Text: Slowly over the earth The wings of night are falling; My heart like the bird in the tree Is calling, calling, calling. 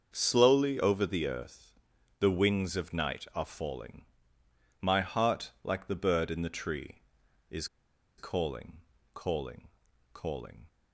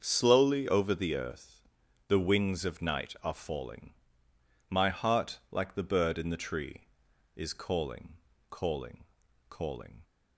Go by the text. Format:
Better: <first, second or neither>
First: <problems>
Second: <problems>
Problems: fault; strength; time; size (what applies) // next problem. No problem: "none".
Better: second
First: starts louder than the rest; until 1.1 s; 6.5 dB // pauses between "earth" and "The"; noticeable; at 1.7 s; 0.46 s long // pauses between "Is" and "calling"; noticeable; at 7.6 s; 0.51 s long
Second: starts louder than the rest; until 1.0 s; 6.5 dB // pauses between "earth" and "The"; noticeable; at 1.6 s; 0.46 s long